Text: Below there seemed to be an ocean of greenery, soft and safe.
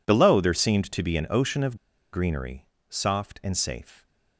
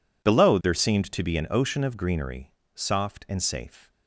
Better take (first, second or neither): second